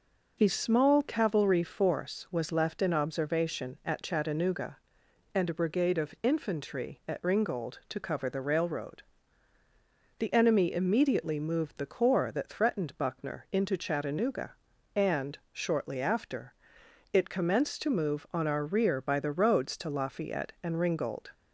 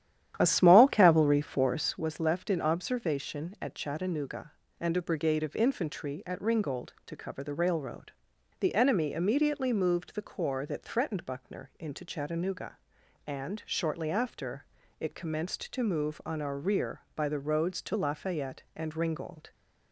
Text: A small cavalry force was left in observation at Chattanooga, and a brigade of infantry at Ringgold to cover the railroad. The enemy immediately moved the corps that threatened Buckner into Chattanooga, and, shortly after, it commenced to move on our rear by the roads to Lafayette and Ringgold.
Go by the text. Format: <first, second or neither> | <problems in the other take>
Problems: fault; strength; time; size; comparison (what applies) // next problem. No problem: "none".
first | starts louder than the rest; strong; until 2.1 s; 11 dB